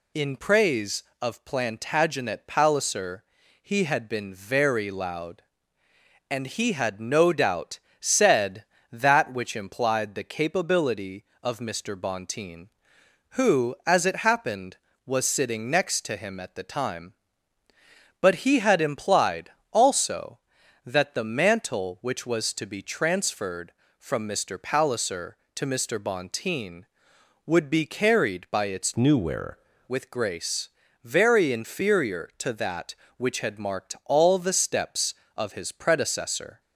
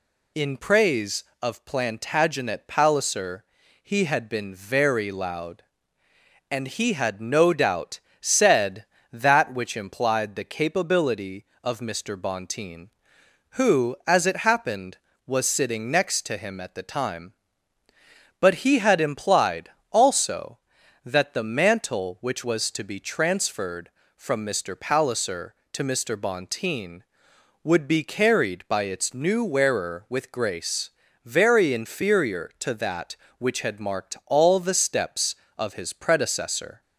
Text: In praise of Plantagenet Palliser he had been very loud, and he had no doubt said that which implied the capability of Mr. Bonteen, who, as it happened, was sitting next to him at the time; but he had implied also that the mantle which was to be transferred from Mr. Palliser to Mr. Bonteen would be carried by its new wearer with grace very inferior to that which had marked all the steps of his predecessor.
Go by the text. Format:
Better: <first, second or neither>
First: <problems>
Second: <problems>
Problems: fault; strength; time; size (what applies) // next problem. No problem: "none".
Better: second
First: pauses between "Palliser" and "he"; at 3.2 s; 0.38 s long // pauses between "doubt" and "said"; slight; at 7.7 s; 0.22 s long // pauses between "implied" and "also"; slight; at 19.5 s; 0.20 s long // changes voice from "new" to "wearer"; from 28.9 to 29.5 s; 0.6 s long // pauses between "grace" and "very"; slight; at 30.6 s; 0.36 s long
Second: pauses between "Palliser" and "he"; at 3.4 s; 0.38 s long // pauses between "doubt" and "said"; slight; at 7.9 s; 0.22 s long // pauses between "implied" and "also"; slight; at 19.7 s; 0.20 s long // pauses between "grace" and "very"; slight; at 30.8 s; 0.36 s long